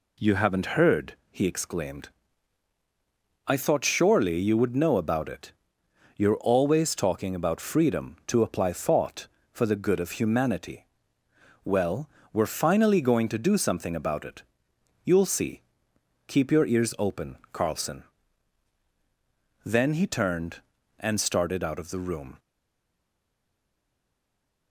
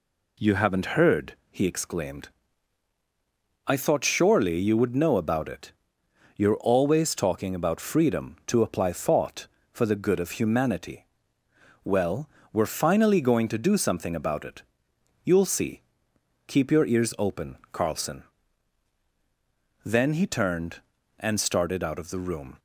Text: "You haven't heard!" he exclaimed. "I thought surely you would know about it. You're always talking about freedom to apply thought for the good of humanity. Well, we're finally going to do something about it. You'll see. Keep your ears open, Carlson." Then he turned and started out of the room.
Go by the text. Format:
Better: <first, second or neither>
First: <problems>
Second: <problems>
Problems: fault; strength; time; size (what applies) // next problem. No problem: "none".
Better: second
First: stays silent after the last word; from 22.3 s on; 2.4 s long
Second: none